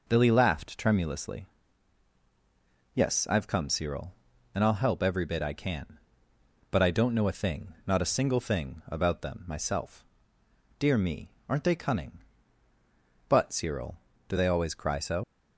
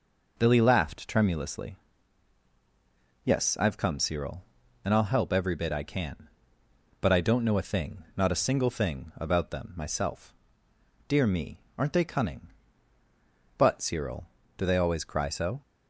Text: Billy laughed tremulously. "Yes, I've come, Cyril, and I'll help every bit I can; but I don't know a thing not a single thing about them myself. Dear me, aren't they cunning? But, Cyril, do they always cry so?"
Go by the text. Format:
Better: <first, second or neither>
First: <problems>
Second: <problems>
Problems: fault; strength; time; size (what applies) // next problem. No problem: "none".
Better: second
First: leaves "so" unfinished; at 15.2 s; 80 ms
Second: none